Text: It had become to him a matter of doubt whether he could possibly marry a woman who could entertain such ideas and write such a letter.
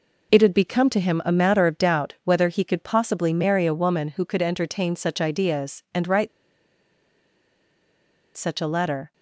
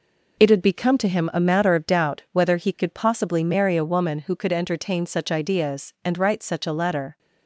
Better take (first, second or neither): second